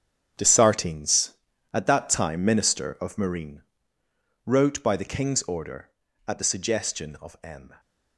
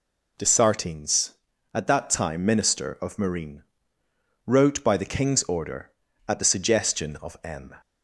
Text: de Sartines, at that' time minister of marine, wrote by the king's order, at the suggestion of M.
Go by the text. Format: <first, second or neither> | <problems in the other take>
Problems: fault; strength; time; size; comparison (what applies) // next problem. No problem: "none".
second | gets quieter; strong; throughout; 11 dB